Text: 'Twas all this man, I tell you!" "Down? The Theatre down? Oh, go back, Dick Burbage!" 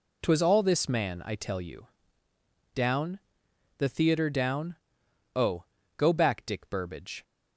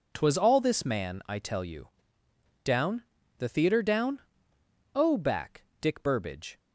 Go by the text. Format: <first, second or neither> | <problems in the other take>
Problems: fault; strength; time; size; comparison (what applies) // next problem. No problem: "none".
first | skips "go"; at 5.1 s